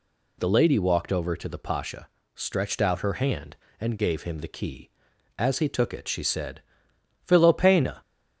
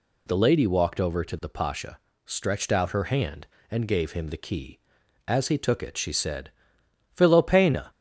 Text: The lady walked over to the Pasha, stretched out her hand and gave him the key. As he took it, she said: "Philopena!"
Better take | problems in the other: neither | none

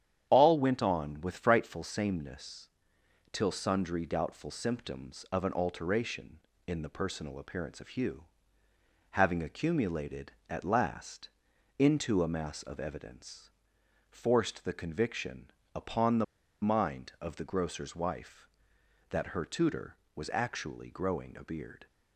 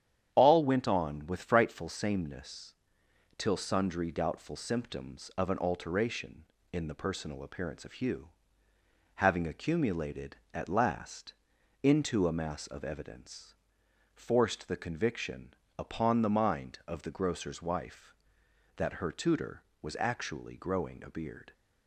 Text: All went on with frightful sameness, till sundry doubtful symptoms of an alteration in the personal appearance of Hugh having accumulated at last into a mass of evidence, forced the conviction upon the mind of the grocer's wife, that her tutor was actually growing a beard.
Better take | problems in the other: second | starts louder than the rest; strong; until 1.2 s; 9.5 dB; strong in the second // pauses between "Hugh" and "having"; noticeable; at 8.2 s; 0.86 s long; noticeable in the second // pauses between "last" and "into"; noticeable; at 11.2 s; 0.50 s long; noticeable in the second // pauses between "conviction" and "upon"; slight; at 15.4 s; 0.24 s long; slight in the second // pauses between "the" and "mind"; at 16.2 s; 0.37 s long

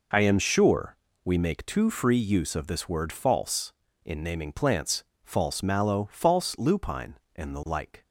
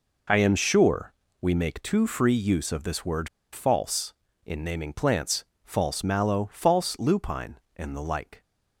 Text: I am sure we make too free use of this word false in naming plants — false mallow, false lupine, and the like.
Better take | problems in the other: first | pauses between "sure" and "we"; slight; at 1.1 s; 0.26 s long; slight in the first // pauses between "word" and "false"; slight; at 3.2 s; 0.26 s long

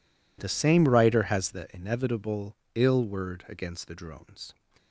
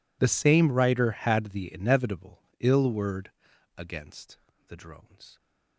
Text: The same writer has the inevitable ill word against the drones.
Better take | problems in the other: first | says "had" for "has"; at 1.1 s // pauses between "inevitable" and "ill"; slight; at 2.4 s; 0.18 s long; slight in the first // pauses between "word" and "against"; noticeable; at 3.3 s; 0.46 s long // pauses between "against" and "the"; slight; at 4.3 s; 0.32 s long

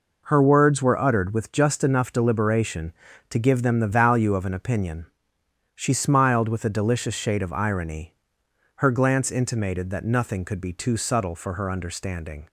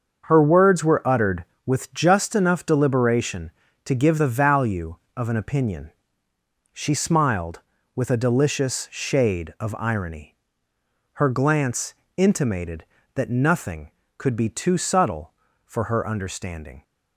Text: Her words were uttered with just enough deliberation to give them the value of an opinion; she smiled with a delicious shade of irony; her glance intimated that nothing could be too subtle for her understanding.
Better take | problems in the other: first | starts louder than the rest; until 1.2 s; 6.5 dB // skips "them"; at 4.1 s // pauses between "glance" and "intimated"; slight; at 11.9 s; 0.22 s long

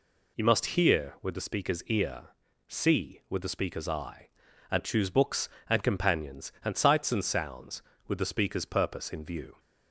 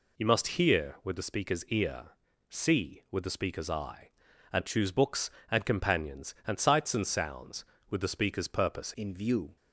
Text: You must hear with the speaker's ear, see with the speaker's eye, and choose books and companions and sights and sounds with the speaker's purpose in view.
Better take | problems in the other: first | changes voice at "in"; from 8.9 s on; 0.6 s long

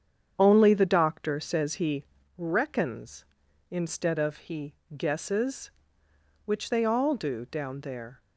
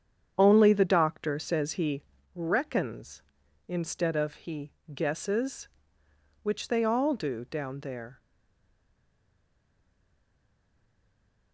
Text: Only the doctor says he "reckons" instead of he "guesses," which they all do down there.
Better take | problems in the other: first | starts louder than the rest; strong; until 1.3 s; 8 dB; strong in the first // pauses between "he" and "reckons"; slight; at 2.0 s; 0.31 s long; slight in the first // pauses between "he" and "guesses"; slight; at 4.7 s; 0.20 s long; slight in the first // stays silent after the last word; strong; from 8.1 s on; 3.4 s long

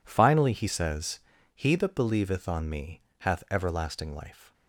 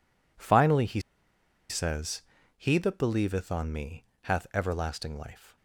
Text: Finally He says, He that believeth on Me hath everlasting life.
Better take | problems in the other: first | pauses between "He" and "says"; noticeable; at 1.0 s; 0.69 s long // pauses between "Me" and "hath"; slight; at 4.0 s; 0.18 s long; slight in the first

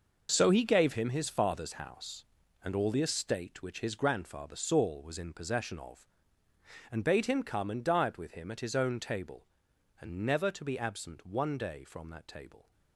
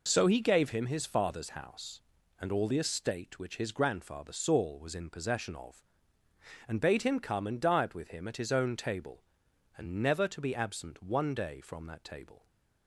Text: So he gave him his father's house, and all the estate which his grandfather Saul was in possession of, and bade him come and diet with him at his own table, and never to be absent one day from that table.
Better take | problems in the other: second | gets quieter; strong; throughout; 11 dB

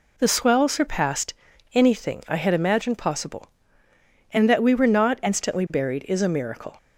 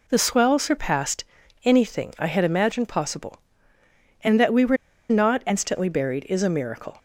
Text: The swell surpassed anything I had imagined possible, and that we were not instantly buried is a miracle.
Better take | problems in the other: first | pauses between "surpassed" and "anything"; at 1.2 s; 0.40 s long; also in the first // pauses between "were" and "not"; slight; at 4.7 s; 0.33 s long

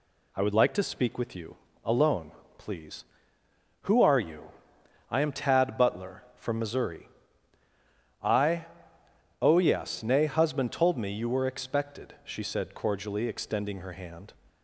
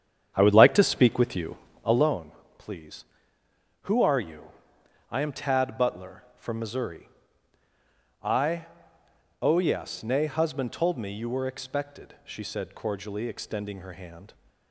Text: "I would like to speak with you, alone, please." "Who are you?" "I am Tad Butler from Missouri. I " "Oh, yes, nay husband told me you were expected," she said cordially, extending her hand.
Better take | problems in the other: first | starts louder than the rest; strong; until 2.1 s; 8.5 dB

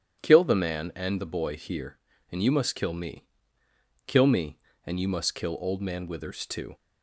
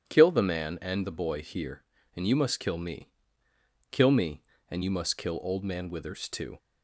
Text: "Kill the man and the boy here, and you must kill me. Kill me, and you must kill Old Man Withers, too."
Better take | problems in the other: neither | starts louder than the rest; strong; the same in both

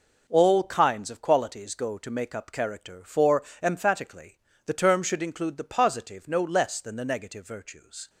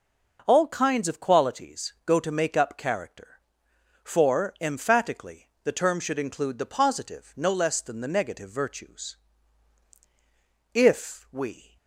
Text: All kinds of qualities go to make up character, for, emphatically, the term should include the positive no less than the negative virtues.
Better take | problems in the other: first | goes on to say "If we"; noticeable; from 10.7 s on; 1.0 s long

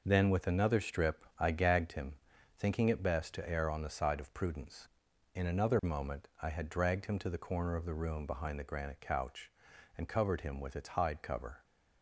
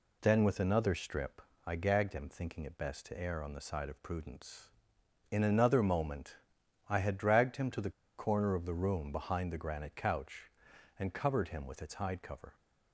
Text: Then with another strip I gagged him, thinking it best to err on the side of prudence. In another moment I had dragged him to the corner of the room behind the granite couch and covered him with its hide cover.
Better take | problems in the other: first | pauses between "strip" and "I"; slight; at 1.4 s; 0.24 s long // pauses between "moment" and "I"; noticeable; at 6.3 s; 0.54 s long // pauses between "the" and "corner"; slight; at 7.9 s; 0.26 s long

